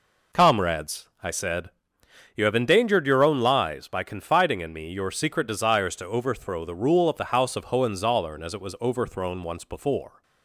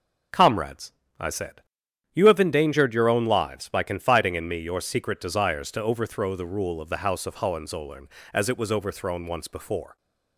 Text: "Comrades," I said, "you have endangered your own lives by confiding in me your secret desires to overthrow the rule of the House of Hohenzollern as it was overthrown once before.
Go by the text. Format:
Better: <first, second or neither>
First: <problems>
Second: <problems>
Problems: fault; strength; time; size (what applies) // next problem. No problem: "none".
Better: neither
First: none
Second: none